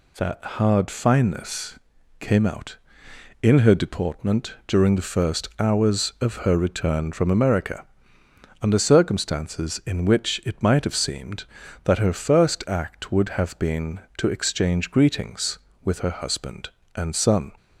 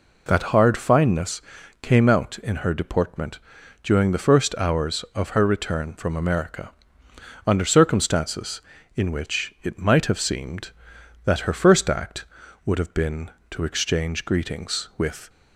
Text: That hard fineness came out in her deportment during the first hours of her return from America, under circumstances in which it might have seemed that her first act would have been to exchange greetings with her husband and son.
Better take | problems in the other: first | pauses between "fineness" and "came"; at 1.4 s; 0.40 s long; also in the first // pauses between "deportment" and "during"; at 3.3 s; 0.42 s long // stops before "her husband and son"; at 15.2 s

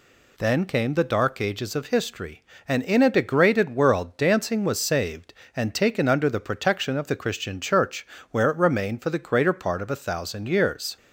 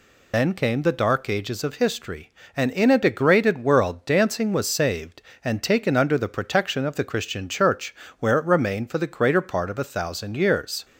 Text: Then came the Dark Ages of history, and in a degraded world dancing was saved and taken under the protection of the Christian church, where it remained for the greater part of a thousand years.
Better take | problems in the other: first | loses the start of "Then"; at 0.3 s; 70 ms

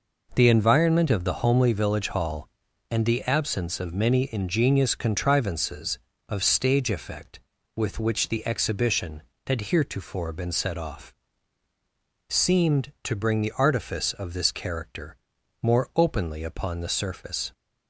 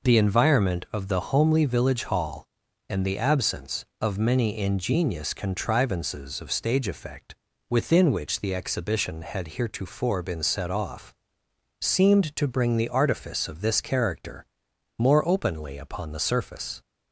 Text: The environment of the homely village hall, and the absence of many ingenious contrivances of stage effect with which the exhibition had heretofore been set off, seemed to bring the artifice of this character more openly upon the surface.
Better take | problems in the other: first | says "within" for "with"; at 7.6 s // pauses between "character" and "more"; noticeable; at 14.4 s; 0.52 s long; noticeable in the first

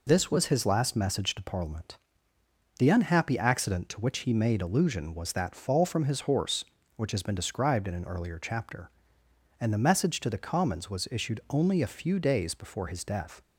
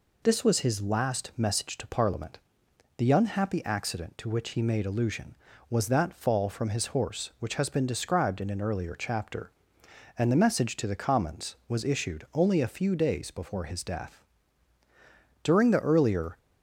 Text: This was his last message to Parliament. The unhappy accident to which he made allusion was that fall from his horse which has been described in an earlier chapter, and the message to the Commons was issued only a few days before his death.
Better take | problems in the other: first | goes on to say "During the earlier"; noticeable; from 15.4 s on; 0.94 s long

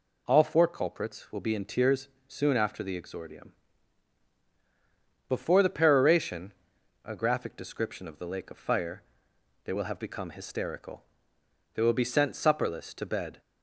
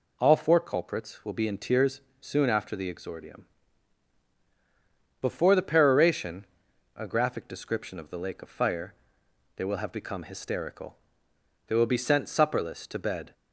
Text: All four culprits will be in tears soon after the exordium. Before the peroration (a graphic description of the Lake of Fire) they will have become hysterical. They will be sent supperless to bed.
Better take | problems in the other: neither | pauses between "tears" and "soon"; slight; the same in both

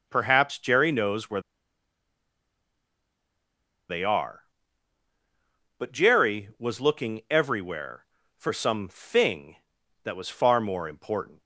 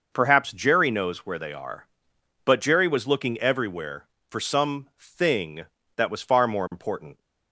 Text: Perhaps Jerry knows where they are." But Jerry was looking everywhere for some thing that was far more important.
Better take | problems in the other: second | pauses between "where" and "they"; strong; at 1.4 s; 2.4 s long

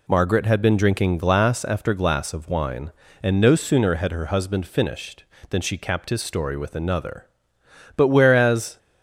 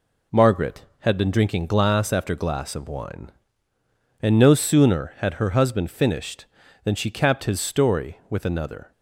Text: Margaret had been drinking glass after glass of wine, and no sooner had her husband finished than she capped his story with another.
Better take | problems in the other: second | goes on to say "But whereas"; noticeable; from 7.9 s on; 0.82 s long

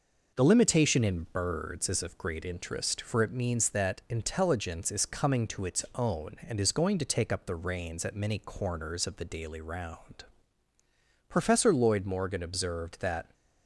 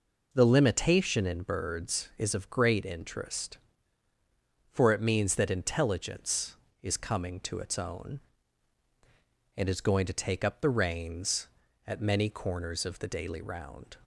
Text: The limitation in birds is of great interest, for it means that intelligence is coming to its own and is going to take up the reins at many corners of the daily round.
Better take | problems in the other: second | goes on to say "Professor Lloyd Morgan observed that"; strong; from 11.2 s on; 2.0 s long

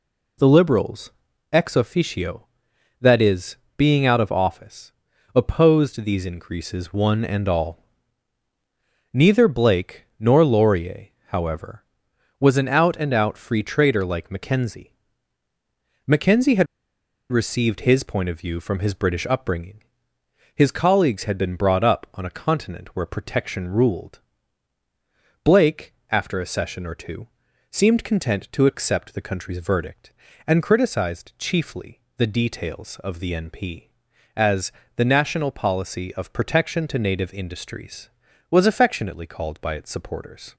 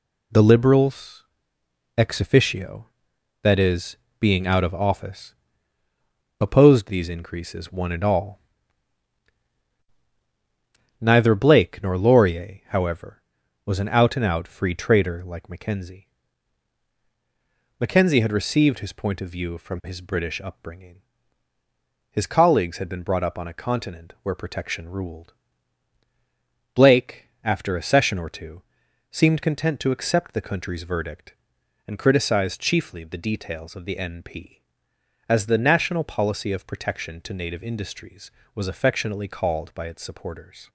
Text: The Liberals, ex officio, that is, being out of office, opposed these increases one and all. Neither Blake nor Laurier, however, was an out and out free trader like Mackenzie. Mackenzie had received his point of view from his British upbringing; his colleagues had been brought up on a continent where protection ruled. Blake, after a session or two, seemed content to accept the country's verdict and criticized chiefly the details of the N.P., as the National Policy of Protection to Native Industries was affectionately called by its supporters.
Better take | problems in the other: second | pauses between "had" and "received"; noticeable; at 16.6 s; 0.66 s long // pauses between "chiefly" and "the"; slight; at 32.0 s; 0.18 s long // pauses between "as" and "the"; slight; at 34.7 s; 0.26 s long

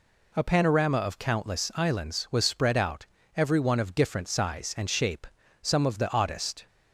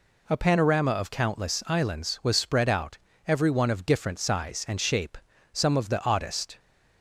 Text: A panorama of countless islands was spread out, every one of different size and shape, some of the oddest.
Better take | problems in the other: neither | none

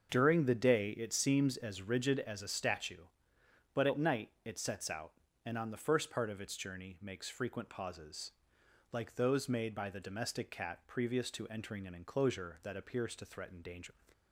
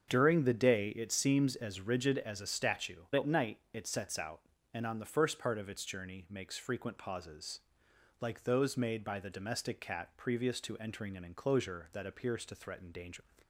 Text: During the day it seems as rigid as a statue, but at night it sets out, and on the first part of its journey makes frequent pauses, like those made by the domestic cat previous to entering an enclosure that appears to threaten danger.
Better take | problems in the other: first | starts louder than the rest; strong; until 1.1 s; 7.5 dB; also in the first // skips "but"; at 3.0 s

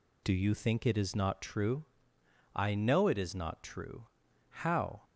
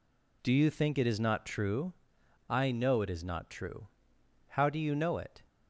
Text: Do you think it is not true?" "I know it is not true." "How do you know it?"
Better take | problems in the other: second | stops before "do you know it"; at 5.0 s

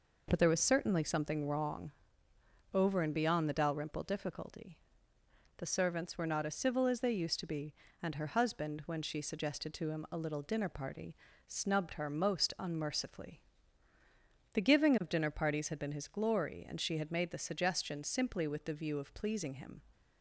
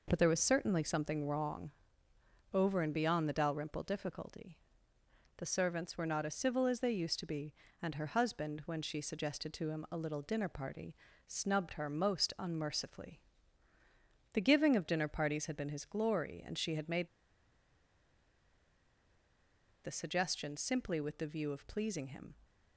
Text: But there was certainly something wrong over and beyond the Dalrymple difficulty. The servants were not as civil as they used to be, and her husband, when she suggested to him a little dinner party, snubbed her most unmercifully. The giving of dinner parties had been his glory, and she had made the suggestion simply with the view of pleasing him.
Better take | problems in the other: first | pauses between "wrong" and "over"; noticeable; at 1.7 s; 0.80 s long; noticeable in the first // pauses between "made" and "the"; strong; at 17.0 s; 2.7 s long

